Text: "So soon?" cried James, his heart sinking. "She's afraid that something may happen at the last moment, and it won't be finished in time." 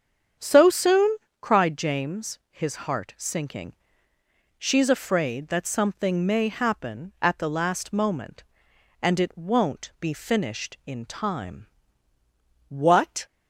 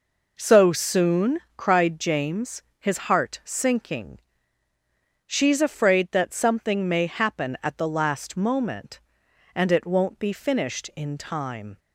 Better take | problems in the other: second | starts louder than the rest; strong; until 1.6 s; 8 dB // goes on to say "What"; from 12.6 s on; 0.56 s long

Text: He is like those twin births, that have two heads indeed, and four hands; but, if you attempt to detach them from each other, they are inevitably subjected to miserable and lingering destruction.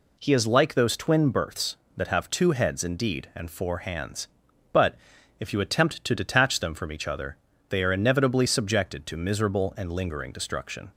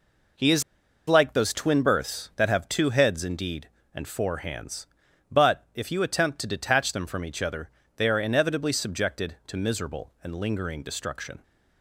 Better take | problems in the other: first | pauses between "is" and "like"; noticeable; at 0.6 s; 0.47 s long

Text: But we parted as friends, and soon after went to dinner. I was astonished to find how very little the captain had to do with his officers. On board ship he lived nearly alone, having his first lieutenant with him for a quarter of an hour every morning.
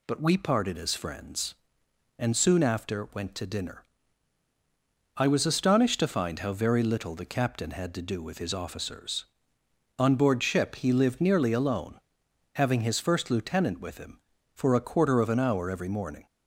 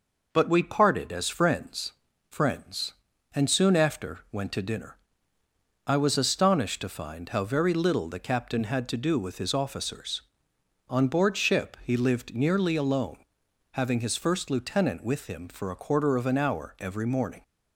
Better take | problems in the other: first | says "friends" twice; at 2.3 s

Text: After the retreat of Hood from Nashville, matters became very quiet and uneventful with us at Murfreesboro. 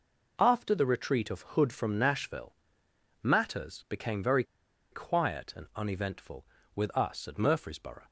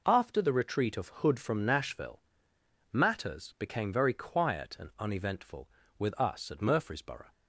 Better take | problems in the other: second | pauses between "very" and "quiet"; noticeable; at 4.4 s; 0.48 s long

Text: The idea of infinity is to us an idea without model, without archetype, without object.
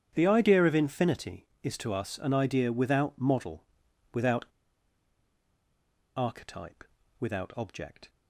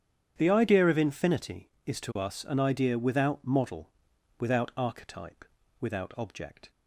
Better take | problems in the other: second | starts louder than the rest; strong; until 1.1 s; 9 dB; strong in the second // pauses between "without" and "archetype"; strong; at 4.4 s; 1.7 s long

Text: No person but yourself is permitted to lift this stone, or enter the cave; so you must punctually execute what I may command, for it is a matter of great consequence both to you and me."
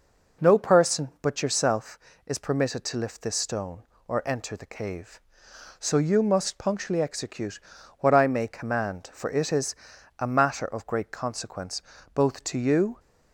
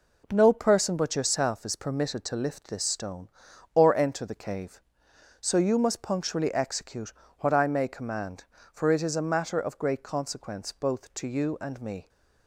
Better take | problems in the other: second | pauses between "execute" and "what"; at 7.5 s; 0.42 s long; slight in the second // pauses between "is" and "a"; at 9.7 s; 0.44 s long // pauses between "consequence" and "both"; slight; at 11.8 s; 0.32 s long // stops before "and me"; at 12.9 s

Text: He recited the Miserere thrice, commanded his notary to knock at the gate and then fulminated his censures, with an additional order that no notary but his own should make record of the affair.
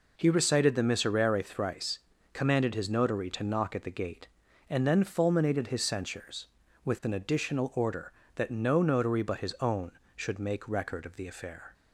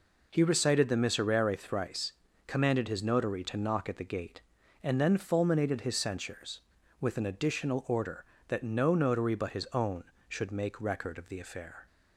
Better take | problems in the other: neither | none

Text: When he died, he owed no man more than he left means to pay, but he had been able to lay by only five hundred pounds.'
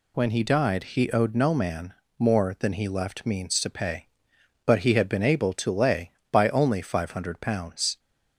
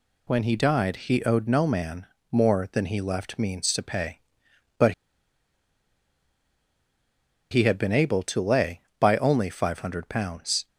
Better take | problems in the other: first | pauses between "man" and "more"; slight; at 2.0 s; 0.24 s long; slight in the first // pauses between "but" and "he"; strong; at 4.9 s; 2.5 s long

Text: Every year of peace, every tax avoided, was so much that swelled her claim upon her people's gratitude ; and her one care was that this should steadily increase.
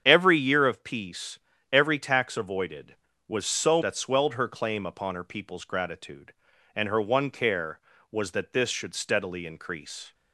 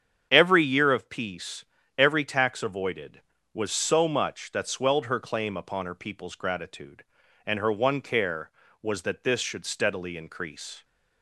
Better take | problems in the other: second | starts louder than the rest; strong; until 1.0 s; 8 dB; strong in the second // skips "much"; at 3.8 s

